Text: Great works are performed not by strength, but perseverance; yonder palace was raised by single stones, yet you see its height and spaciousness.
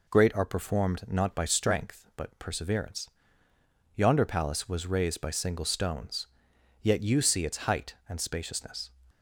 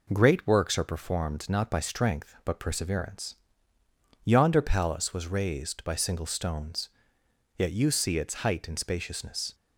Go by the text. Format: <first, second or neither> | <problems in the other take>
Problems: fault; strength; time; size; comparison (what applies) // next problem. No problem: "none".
second | skips "works"; at 0.3 s